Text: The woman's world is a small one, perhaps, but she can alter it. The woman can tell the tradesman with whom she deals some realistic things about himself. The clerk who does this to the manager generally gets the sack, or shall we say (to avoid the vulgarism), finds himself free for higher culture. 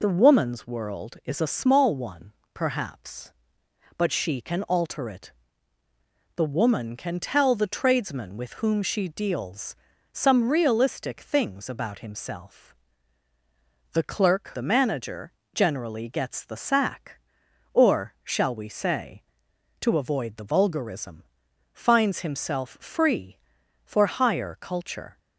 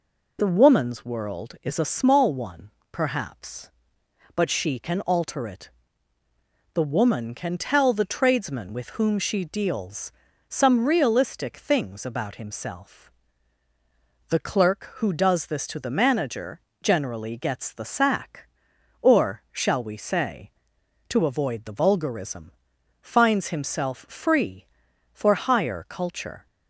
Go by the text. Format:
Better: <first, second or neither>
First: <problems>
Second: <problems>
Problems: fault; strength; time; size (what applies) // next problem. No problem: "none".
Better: second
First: pauses between "deals" and "some"; slight; at 9.7 s; 0.36 s long // skips "who does this to"; at 14.5 s // pauses between "manager" and "generally"; slight; at 15.3 s; 0.24 s long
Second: pauses between "deals" and "some"; slight; at 10.1 s; 0.36 s long // pauses between "manager" and "generally"; slight; at 16.6 s; 0.24 s long